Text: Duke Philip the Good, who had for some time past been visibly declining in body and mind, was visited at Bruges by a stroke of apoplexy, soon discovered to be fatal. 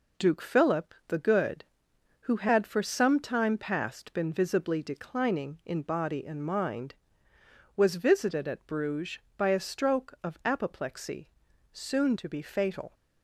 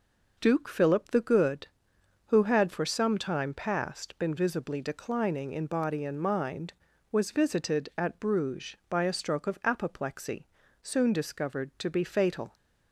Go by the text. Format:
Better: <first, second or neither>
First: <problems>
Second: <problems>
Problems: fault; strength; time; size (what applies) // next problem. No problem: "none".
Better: second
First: skips "discovered"; at 12.1 s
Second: none